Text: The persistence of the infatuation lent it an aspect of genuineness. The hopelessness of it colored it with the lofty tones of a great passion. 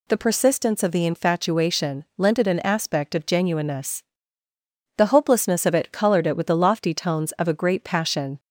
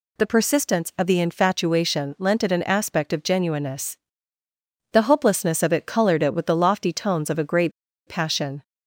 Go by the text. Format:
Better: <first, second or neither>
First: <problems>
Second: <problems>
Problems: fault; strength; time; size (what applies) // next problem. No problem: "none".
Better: first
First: none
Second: pauses between "great" and "passion"; at 7.7 s; 0.37 s long